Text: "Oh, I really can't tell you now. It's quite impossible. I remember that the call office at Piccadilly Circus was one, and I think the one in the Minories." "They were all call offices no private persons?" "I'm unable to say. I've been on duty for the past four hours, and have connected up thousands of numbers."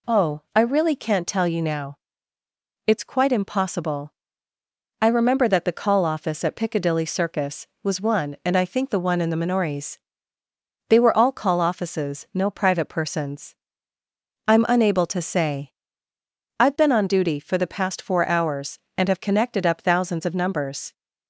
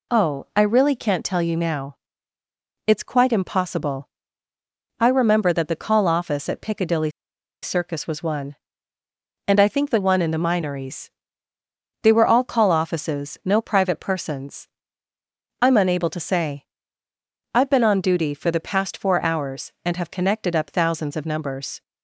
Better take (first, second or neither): first